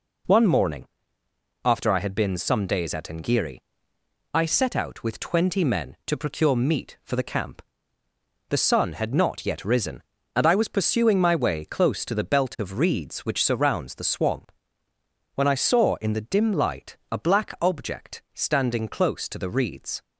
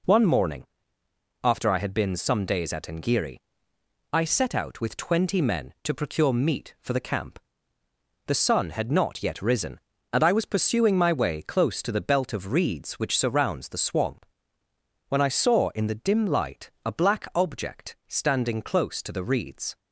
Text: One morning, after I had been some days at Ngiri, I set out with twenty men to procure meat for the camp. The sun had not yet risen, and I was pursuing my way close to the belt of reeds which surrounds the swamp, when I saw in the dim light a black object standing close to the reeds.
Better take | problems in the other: neither | pauses between "light" and "a"; slight; the same in both

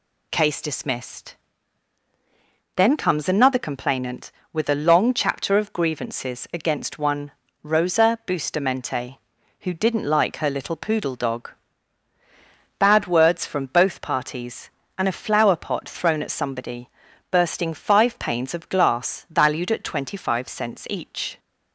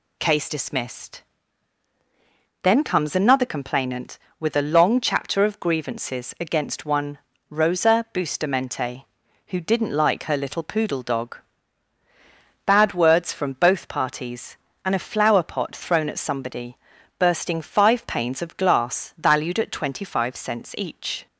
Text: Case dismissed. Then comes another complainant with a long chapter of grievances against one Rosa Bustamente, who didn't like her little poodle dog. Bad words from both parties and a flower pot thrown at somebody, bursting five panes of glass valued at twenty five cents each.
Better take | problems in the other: neither | pauses between "one" and "Rosa"; slight; the same in both

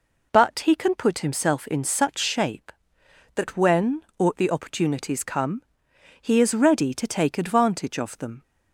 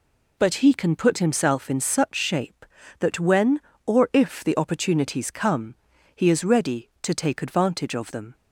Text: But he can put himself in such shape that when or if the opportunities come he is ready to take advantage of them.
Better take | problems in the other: second | skips "if"; at 4.3 s // pauses between "come" and "he"; noticeable; at 5.6 s; 0.58 s long; also in the second

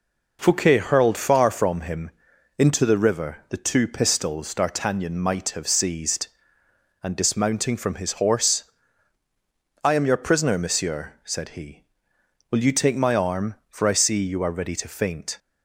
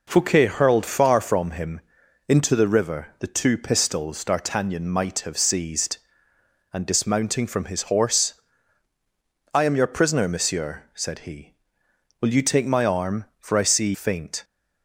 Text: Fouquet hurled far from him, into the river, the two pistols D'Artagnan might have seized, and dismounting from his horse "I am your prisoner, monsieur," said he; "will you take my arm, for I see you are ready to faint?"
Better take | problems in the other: first | pauses between "horse" and "I"; at 8.3 s; 1.2 s long; also in the first // skips "you are ready to"; at 13.9 s

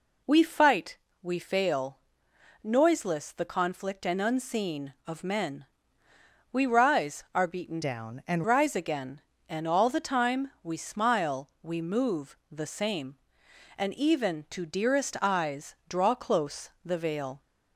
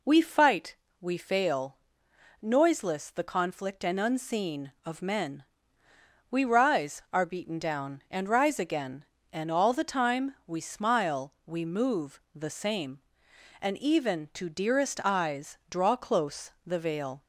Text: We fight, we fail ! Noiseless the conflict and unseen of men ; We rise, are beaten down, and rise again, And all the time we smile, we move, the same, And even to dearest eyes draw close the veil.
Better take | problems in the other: second | changes voice from "down" to "and"; from 7.8 to 8.4 s; 0.6 s long

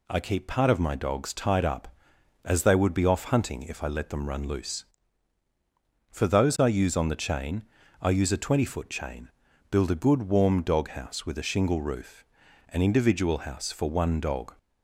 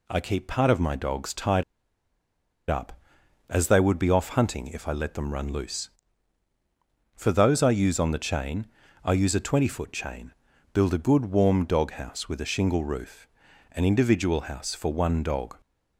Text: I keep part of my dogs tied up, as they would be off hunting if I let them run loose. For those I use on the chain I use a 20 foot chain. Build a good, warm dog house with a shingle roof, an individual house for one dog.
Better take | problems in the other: first | pauses between "tied" and "up"; at 1.6 s; 1.0 s long // pauses between "chain" and "I"; slight; at 8.6 s; 0.34 s long; slight in the first

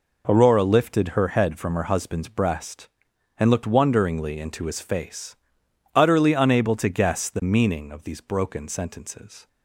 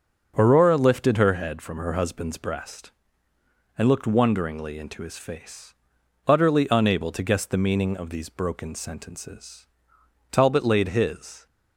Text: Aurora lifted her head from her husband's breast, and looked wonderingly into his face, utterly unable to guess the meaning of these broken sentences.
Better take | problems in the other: first | starts louder than the rest; until 1.3 s; 6.5 dB // goes on to say "Talbot laid his"; noticeable; from 10.3 s on; 1.1 s long

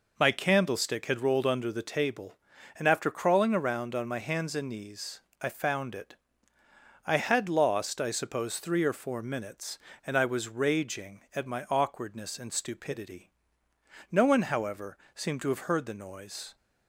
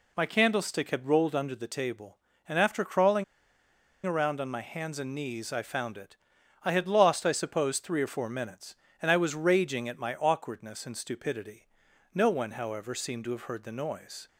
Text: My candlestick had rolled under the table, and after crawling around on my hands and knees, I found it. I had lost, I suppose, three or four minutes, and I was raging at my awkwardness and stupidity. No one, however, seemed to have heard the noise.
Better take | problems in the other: first | pauses between "crawling" and "around"; noticeable; at 3.2 s; 0.81 s long

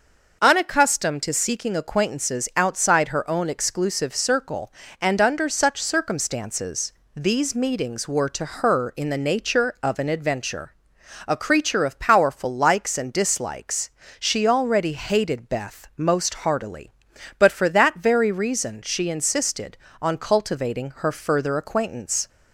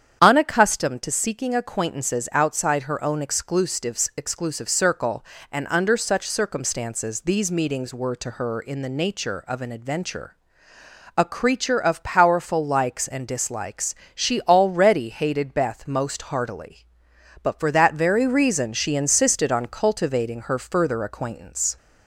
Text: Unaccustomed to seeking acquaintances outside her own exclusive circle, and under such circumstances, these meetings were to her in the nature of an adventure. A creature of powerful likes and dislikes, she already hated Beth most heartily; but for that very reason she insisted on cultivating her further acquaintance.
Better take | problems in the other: first | starts louder than the rest; strong; until 1.2 s; 8.5 dB // says "exclusive" twice; at 4.1 s

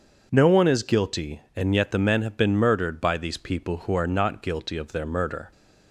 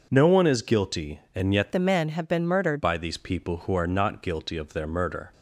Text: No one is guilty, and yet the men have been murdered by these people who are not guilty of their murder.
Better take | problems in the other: first | changes voice from "the" to "murdered"; from 1.7 to 2.8 s; 1.1 s long

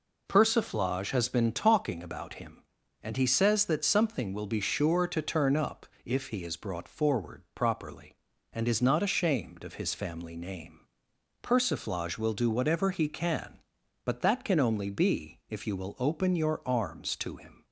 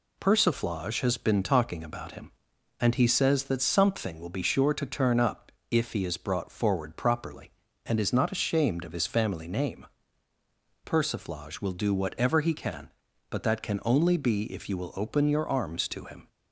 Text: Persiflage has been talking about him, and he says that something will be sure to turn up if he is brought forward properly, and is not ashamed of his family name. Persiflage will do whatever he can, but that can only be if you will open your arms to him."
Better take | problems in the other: neither | pauses between "up" and "if"; slight; the same in both

